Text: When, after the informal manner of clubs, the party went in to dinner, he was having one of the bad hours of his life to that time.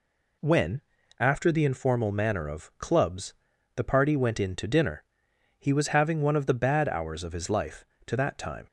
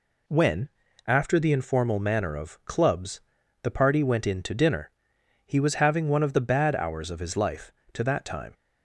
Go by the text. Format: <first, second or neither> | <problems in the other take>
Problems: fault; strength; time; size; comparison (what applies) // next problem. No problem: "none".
neither | none